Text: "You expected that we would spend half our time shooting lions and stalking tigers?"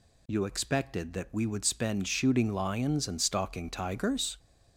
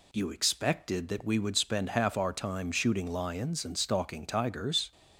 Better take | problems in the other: second | skips "half our time"; at 2.0 s

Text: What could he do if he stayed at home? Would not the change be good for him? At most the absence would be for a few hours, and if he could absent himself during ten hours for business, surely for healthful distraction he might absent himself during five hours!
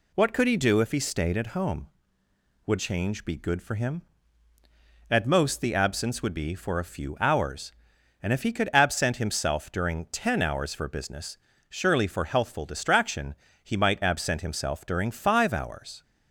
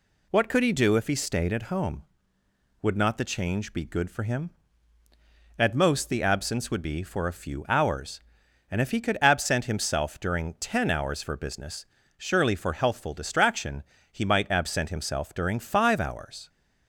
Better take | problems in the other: second | skips "not the"; at 2.7 s // pauses between "distraction" and "he"; slight; at 13.3 s; 0.30 s long; slight in the second

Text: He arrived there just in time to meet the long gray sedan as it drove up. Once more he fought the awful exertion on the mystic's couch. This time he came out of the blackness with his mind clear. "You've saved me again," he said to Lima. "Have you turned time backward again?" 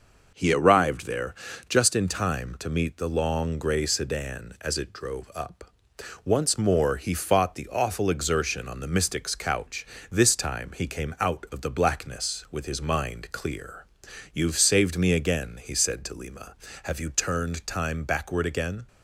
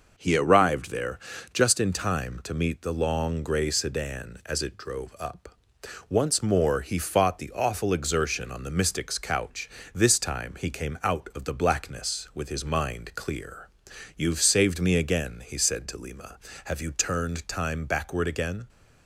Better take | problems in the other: neither | pauses between "there" and "just"; slight; the same in both

